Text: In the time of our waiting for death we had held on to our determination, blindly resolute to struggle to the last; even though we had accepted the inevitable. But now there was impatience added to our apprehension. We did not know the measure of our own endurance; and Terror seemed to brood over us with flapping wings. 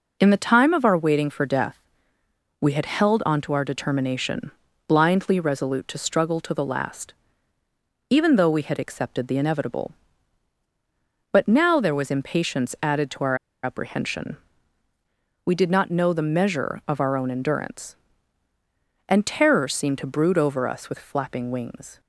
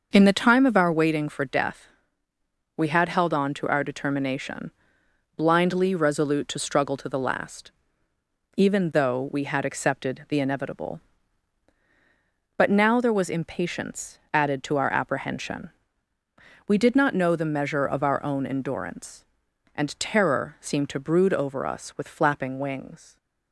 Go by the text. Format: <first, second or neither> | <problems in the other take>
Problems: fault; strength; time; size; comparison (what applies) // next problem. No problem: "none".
second | pauses between "death" and "we"; noticeable; at 1.7 s; 0.82 s long; noticeable in the second // pauses between "our" and "apprehension"; slight; at 13.3 s; 0.27 s long